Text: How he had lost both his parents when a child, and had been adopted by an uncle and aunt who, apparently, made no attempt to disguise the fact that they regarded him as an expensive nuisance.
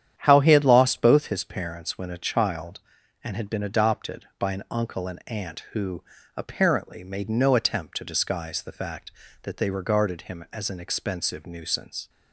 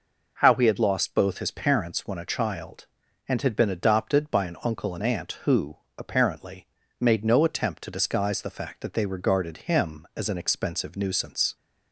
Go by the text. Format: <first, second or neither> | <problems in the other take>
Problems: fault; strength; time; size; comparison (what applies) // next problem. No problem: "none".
second | starts louder than the rest; strong; until 1.4 s; 9.5 dB